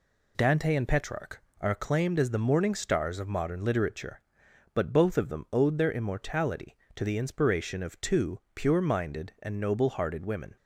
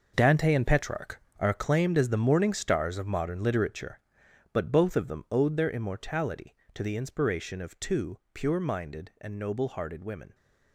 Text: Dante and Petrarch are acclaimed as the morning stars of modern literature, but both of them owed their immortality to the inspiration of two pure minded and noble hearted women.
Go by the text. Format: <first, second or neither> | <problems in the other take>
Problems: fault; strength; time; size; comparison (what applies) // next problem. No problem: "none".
first | gets quieter; strong; throughout; 12 dB